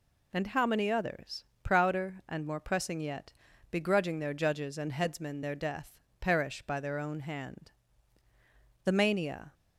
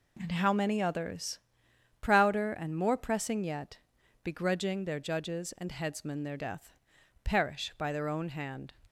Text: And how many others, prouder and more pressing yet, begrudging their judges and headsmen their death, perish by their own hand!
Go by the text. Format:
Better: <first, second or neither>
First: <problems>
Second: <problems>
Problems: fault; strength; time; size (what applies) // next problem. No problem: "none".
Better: second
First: goes on to say "The mania"; noticeable; from 8.8 s on; 0.70 s long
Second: none